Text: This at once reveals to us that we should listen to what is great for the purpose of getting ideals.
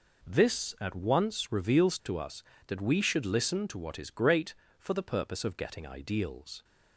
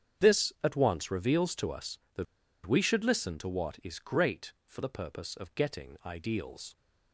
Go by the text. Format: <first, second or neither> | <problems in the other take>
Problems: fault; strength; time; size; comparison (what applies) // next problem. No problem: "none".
first | starts louder than the rest; strong; until 1.3 s; 8 dB // pauses between "that" and "we"; at 2.2 s; 0.41 s long